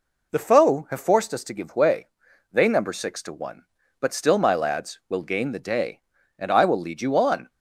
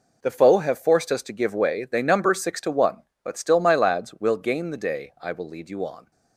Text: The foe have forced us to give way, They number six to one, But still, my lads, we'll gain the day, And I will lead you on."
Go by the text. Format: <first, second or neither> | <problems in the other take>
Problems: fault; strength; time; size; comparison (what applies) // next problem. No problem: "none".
first | skips "And"; at 5.1 s